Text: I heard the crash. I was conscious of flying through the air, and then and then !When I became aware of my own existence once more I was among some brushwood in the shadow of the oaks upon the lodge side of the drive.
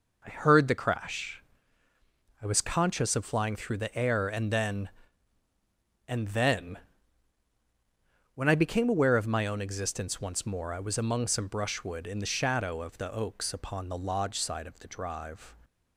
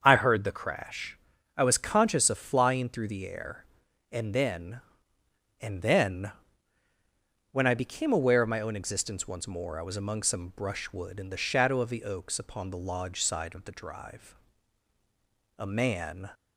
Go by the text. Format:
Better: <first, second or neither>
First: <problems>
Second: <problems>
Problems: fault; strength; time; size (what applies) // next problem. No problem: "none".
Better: first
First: none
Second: starts louder than the rest; until 1.0 s; 7 dB // goes on to say "A man"; noticeable; from 15.5 s on; 0.72 s long